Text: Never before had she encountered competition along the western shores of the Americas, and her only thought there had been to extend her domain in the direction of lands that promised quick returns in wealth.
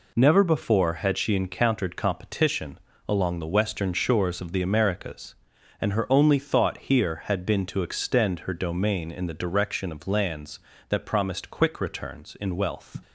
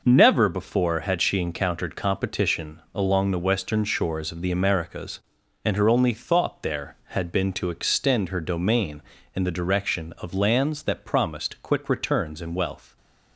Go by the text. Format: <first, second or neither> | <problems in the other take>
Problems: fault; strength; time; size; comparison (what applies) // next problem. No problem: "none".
second | pauses between "competition" and "along"; slight; at 2.7 s; 0.30 s long // says "here" for "there"; at 6.7 s